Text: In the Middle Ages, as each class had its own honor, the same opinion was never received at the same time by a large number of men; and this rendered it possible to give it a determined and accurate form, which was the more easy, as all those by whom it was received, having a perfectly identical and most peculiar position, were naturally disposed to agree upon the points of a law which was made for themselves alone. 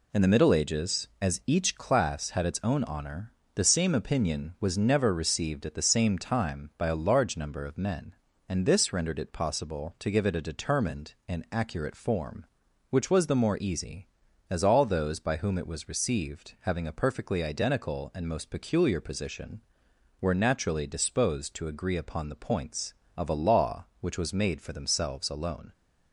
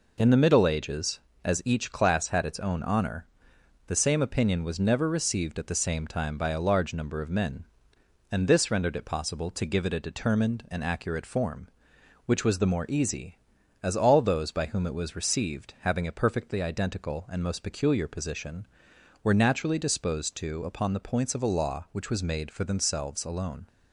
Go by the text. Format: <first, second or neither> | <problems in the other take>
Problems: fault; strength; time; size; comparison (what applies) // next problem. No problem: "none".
first | skips "agree"; at 20.6 s